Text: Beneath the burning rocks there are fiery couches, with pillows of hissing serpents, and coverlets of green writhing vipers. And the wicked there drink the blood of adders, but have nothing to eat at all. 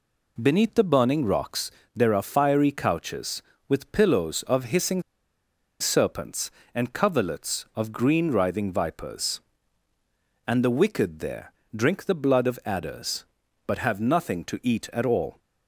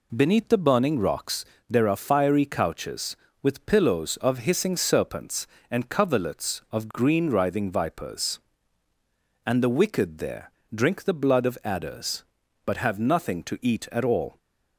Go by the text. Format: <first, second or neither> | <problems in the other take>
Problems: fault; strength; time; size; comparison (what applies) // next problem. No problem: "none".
second | pauses between "rocks" and "there"; slight; at 1.7 s; 0.24 s long; slight in the second // pauses between "hissing" and "serpents"; noticeable; at 5.0 s; 0.79 s long // pauses between "there" and "drink"; slight; at 11.5 s; 0.22 s long; slight in the second